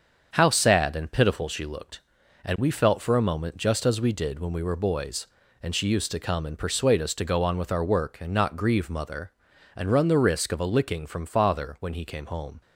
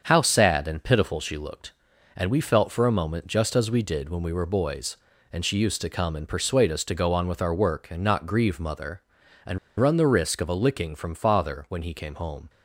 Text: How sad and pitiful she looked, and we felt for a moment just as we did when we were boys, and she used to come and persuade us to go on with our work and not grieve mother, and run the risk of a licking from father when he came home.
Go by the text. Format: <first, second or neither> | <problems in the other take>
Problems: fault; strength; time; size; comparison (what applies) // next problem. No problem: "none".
first | starts louder than the rest; until 1.0 s; 7 dB; also in the first // pauses between "and" and "run"; slight; at 9.5 s; 0.20 s long